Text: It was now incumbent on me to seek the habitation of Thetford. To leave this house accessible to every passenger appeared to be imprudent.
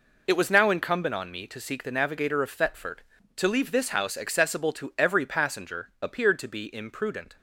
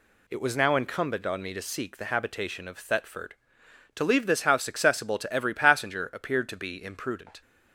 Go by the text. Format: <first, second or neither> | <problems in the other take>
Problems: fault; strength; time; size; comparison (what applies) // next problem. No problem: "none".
second | says "navigator" for "habitation"; at 1.9 s